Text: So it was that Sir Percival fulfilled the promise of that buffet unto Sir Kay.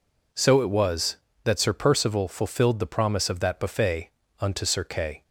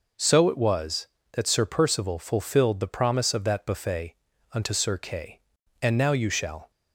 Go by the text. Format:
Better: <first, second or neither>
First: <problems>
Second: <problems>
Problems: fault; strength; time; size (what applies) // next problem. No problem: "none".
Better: first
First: pauses between "buffet" and "unto"; slight; at 4.0 s; 0.30 s long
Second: pauses between "buffet" and "unto"; at 4.1 s; 0.38 s long // goes on to say "And now you shall"; noticeable; from 5.8 s on; 0.88 s long